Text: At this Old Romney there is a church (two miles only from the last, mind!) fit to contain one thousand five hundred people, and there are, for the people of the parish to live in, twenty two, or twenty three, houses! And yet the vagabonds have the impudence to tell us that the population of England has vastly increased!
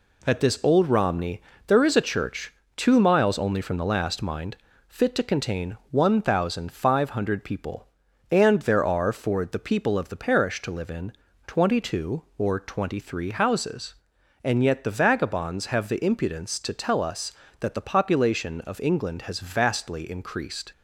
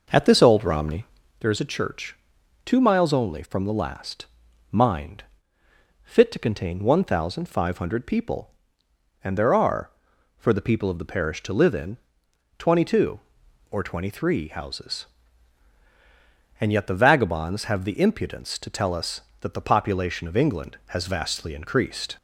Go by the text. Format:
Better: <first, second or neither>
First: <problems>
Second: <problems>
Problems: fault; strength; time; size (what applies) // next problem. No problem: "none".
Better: first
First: pauses between "Romney" and "there"; slight; at 1.4 s; 0.26 s long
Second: starts louder than the rest; noticeable; until 1.4 s; 5.5 dB // pauses between "Romney" and "there"; slight; at 1.0 s; 0.36 s long